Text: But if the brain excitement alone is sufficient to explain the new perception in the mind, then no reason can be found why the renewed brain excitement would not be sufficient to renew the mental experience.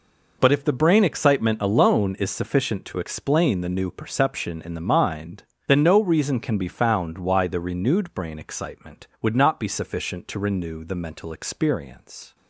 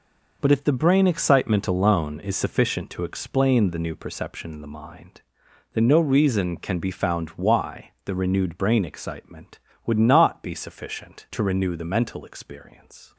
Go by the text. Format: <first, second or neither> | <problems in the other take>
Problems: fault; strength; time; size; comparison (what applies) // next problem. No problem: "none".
neither | none